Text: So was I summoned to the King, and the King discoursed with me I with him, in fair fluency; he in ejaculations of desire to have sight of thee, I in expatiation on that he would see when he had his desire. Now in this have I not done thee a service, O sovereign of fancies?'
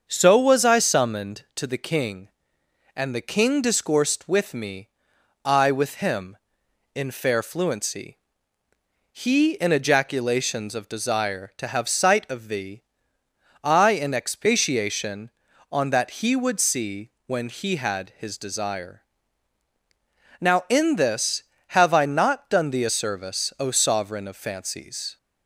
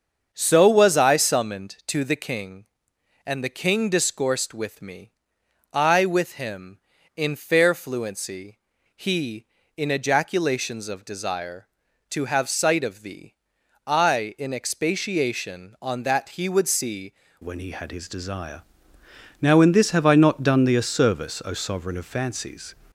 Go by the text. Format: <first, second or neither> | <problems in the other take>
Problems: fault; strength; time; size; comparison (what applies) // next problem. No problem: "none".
first | starts louder than the rest; until 1.3 s; 7 dB; also in the first // pauses between "me" and "I"; noticeable; at 5.1 s; 0.60 s long; noticeable in the first // changes voice at "when"; from 17.4 s on; 5.3 s long